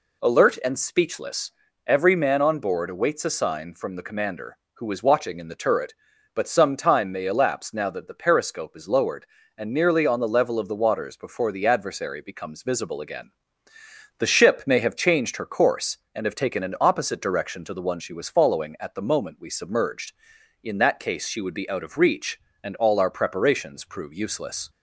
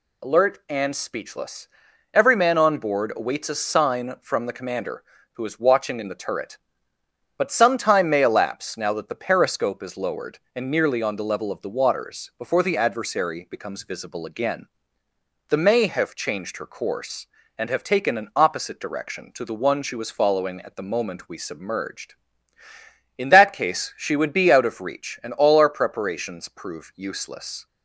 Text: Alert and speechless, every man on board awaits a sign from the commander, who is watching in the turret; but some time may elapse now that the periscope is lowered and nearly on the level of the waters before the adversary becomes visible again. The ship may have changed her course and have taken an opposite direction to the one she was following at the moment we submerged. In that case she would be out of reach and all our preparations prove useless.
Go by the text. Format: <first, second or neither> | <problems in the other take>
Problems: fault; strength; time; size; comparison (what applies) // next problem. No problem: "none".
first | skips "ship"; at 15.5 s